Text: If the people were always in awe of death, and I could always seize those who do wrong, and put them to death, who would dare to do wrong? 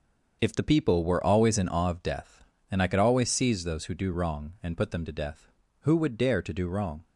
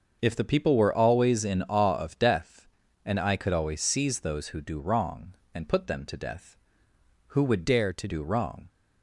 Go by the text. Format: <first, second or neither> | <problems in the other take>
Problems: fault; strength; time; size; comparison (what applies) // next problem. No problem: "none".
first | starts louder than the rest; until 1.2 s; 6.5 dB; also in the first // changes voice from "dare" to "to"; from 7.6 to 8.0 s; 0.4 s long